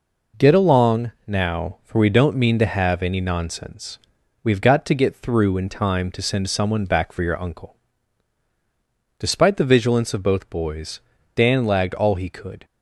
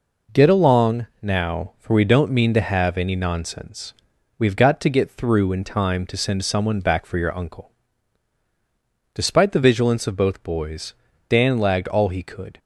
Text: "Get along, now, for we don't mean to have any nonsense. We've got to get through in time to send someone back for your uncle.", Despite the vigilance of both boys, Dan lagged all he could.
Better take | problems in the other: neither | none

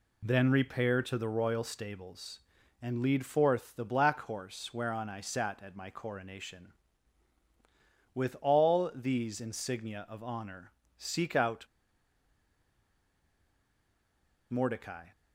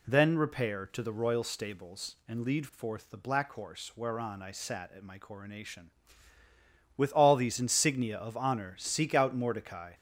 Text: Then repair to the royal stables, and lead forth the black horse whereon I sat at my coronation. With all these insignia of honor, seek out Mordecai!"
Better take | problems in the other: second | pauses between "out" and "Mordecai"; strong; at 11.6 s; 2.8 s long

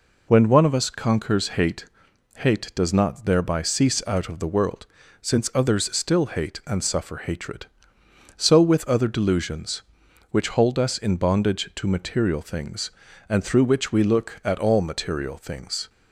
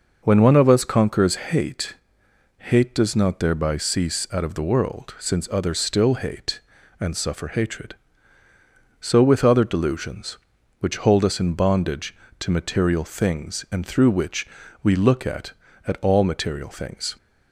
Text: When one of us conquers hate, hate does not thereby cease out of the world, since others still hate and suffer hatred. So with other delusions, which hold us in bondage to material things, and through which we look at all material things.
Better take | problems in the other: first | pauses between "which" and "we"; slight; at 14.4 s; 0.34 s long // says "at" twice; at 15.8 s

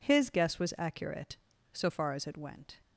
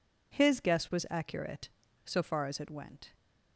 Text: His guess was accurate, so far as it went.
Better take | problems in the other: neither | none

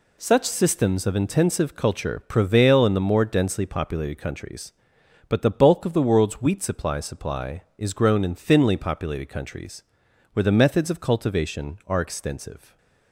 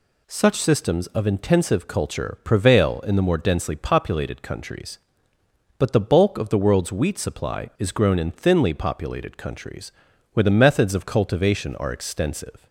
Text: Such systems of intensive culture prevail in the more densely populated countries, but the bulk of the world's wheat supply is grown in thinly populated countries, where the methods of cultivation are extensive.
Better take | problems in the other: second | says "supply" twice; at 7.0 s

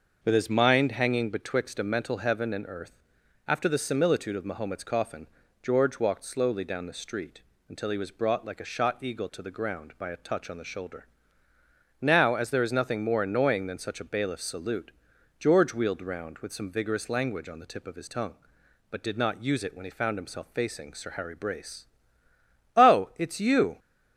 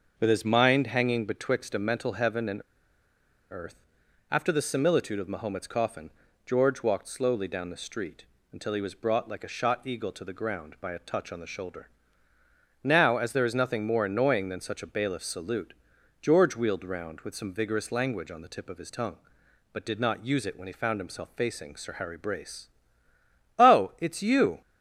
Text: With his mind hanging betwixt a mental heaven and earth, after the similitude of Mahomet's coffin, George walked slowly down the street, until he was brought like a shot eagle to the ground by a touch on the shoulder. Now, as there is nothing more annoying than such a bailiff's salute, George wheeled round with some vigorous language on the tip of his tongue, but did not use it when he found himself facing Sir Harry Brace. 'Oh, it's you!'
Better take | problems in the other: first | starts louder than the rest; until 1.2 s; 6 dB; also in the first // pauses between "and" and "earth"; noticeable; at 2.6 s; 0.90 s long

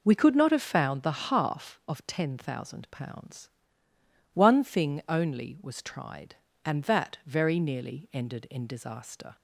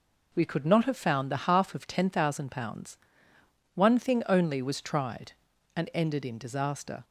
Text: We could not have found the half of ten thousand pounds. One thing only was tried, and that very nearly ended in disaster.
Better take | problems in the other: first | skips "that very nearly"; at 5.9 s

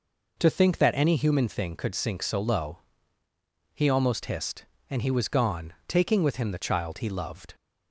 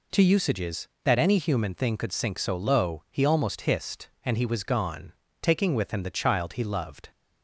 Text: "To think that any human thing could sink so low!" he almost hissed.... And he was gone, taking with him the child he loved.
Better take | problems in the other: first | says "usages" for "think"; at 0.2 s

